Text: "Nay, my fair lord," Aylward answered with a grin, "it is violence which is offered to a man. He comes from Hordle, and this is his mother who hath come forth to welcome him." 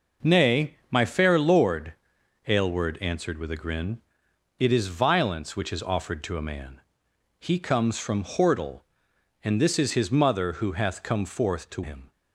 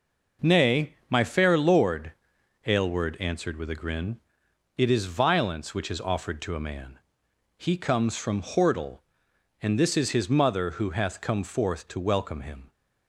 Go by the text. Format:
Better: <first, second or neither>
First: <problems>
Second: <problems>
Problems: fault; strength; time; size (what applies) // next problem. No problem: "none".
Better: second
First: skips "welcome"; at 11.8 s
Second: none